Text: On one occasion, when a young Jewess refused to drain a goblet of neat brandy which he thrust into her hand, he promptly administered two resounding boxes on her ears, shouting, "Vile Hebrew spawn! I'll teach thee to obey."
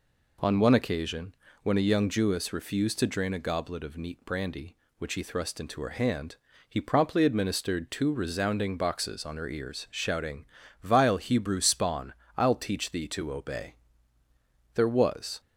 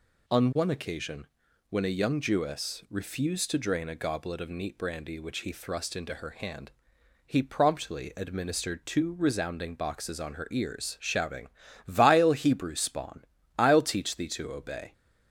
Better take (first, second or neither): second